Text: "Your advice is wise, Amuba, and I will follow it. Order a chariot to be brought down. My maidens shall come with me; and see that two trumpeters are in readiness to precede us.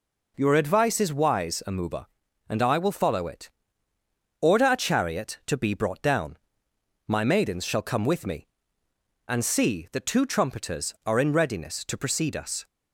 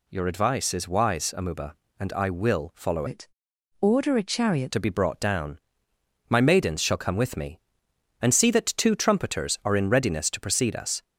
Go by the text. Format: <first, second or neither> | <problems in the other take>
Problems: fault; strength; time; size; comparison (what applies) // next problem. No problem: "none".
first | changes voice from "it" to "chariot"; from 3.0 to 4.7 s; 1.7 s long